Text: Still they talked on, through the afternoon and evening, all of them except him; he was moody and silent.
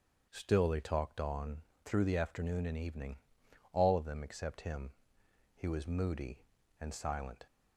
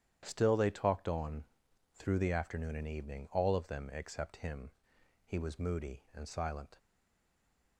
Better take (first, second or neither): first